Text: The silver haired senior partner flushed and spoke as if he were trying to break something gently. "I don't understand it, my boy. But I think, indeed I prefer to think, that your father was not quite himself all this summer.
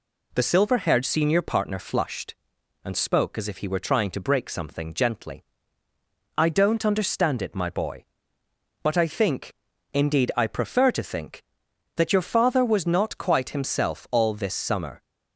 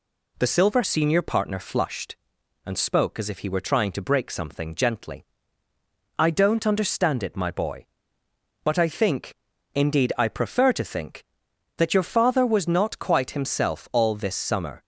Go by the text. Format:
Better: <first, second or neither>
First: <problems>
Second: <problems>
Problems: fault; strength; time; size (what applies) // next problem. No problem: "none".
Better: first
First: none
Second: skips "haired"; at 0.8 s